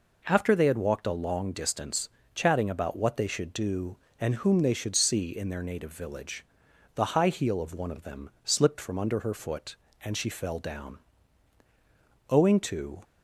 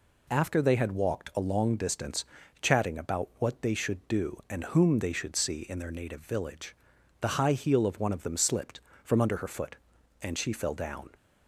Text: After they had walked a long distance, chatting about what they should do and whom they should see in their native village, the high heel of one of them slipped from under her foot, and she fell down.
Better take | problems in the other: second | goes on to say "Owing to"; noticeable; from 12.3 s on; 0.72 s long

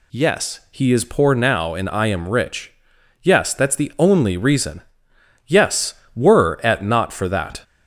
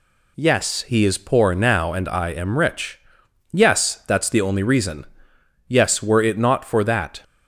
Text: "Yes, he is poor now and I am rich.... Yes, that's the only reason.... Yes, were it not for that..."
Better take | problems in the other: second | says "at" for "it"; at 6.6 s

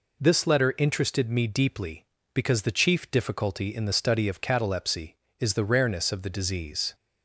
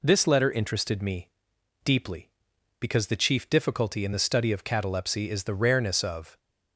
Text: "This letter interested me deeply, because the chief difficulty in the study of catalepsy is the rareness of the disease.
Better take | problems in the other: first | pauses between "me" and "deeply"; noticeable; at 1.2 s; 0.54 s long // stops before "the disease"; at 6.3 s

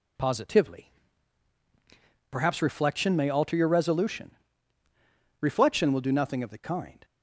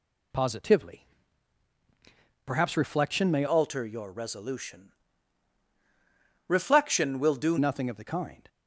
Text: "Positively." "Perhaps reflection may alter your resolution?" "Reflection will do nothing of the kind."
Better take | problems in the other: first | changes voice from "alter" to "do"; from 3.4 to 7.5 s; 4.1 s long

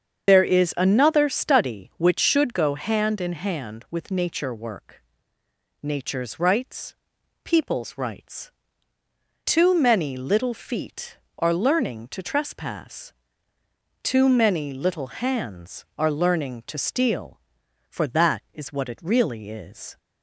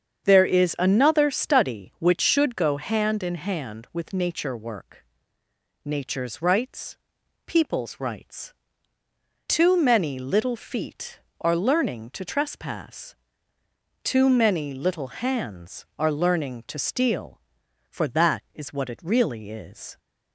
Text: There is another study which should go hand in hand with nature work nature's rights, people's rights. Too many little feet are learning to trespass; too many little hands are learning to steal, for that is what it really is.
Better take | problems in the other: second | loses the start of "There"; at 0.2 s; 40 ms // starts louder than the rest; strong; until 1.3 s; 7 dB; strong in the second // pauses between "work" and "nature's"; noticeable; at 5.0 s; 0.80 s long; noticeable in the second

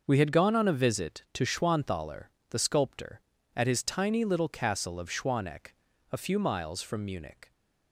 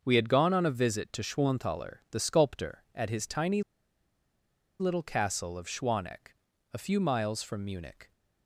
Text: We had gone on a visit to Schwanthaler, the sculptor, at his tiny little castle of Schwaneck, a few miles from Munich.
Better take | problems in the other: first | starts louder than the rest; until 1.0 s; 6.5 dB; also in the first // pauses between "tiny" and "little"; at 3.6 s; 1.1 s long

